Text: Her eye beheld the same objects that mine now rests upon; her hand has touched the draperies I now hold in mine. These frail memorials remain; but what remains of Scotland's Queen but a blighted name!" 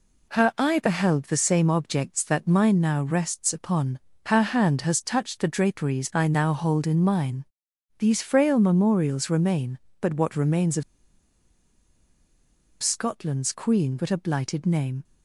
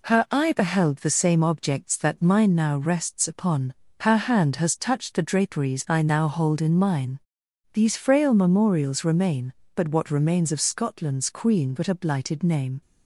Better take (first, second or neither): second